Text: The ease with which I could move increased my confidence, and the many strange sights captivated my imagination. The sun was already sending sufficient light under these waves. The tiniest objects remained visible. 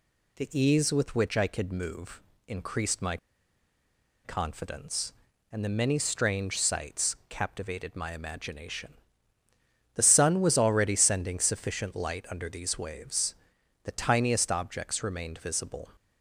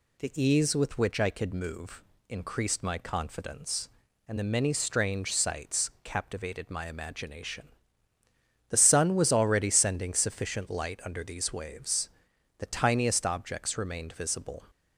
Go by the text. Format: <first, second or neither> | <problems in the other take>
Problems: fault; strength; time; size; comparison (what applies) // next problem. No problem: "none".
second | pauses between "move" and "increased"; slight; at 2.2 s; 0.24 s long; slight in the second // pauses between "my" and "confidence"; at 3.1 s; 1.0 s long